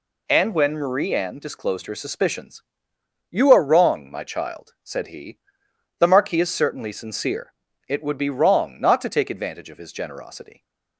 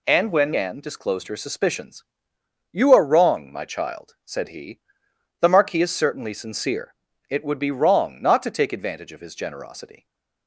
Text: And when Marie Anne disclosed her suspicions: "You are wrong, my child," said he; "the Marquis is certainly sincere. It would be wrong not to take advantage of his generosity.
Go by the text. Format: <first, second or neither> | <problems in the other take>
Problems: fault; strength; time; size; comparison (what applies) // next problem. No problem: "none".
first | skips "Marie"; at 0.5 s // stays silent after the last word; slight; from 9.9 s on; 0.5 s long